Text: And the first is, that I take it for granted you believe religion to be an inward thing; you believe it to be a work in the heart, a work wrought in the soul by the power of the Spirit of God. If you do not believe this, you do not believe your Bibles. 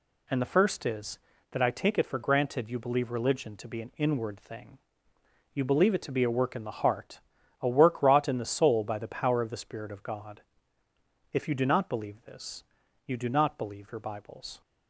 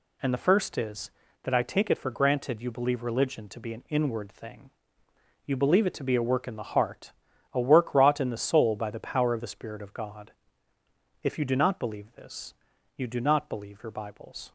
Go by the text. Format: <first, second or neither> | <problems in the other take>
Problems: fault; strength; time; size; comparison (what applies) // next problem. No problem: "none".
neither | none